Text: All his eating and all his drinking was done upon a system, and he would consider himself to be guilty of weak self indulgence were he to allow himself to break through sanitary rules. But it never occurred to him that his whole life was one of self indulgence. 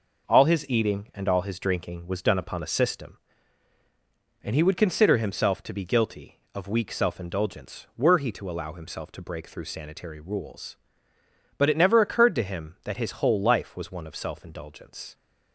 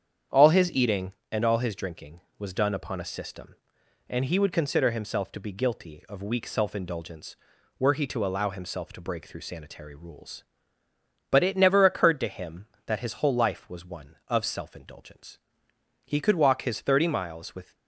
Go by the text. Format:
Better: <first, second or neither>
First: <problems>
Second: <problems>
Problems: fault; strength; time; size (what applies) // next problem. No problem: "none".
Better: first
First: none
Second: starts louder than the rest; strong; until 1.4 s; 8.5 dB // goes on to say "He could walk his thirty miles with"; strong; from 16.0 s on; 1.7 s long